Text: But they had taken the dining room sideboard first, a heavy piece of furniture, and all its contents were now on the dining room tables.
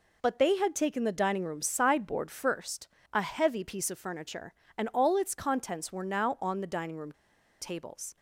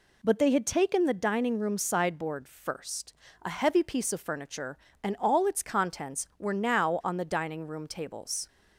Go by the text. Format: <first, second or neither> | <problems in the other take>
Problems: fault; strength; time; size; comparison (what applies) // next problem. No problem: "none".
second | pauses between "room" and "tables"; noticeable; at 7.1 s; 0.48 s long